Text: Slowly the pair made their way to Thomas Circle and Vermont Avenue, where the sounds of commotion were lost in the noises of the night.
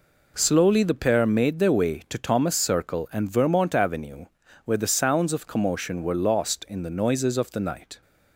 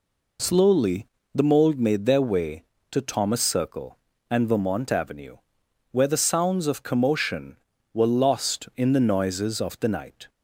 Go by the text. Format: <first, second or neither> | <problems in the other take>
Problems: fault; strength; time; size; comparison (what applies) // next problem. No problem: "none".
first | pauses between "Slowly" and "the"; slight; at 1.0 s; 0.28 s long // says "mold" for "pair"; at 1.4 s